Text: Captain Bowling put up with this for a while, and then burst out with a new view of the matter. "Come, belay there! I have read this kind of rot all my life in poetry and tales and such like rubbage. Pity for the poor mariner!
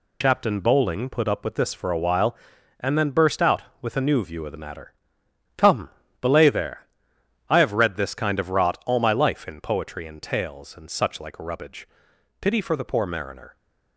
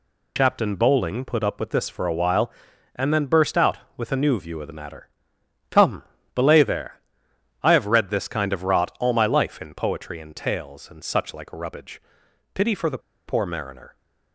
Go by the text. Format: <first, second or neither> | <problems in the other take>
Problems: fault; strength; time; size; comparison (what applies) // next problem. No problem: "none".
first | pauses between "the" and "poor"; slight; at 12.9 s; 0.28 s long